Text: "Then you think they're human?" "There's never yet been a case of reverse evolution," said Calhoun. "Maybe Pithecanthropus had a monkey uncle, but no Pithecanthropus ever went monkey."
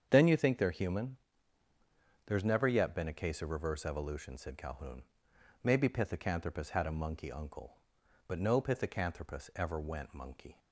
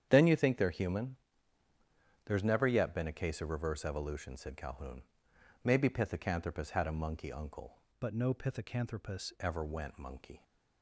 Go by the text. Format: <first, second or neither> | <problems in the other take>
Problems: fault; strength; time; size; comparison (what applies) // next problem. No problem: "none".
first | starts louder than the rest; strong; until 1.1 s; 9 dB; strong in the first // changes voice from "but" to "Pithecanthropus"; from 7.9 to 9.3 s; 1.4 s long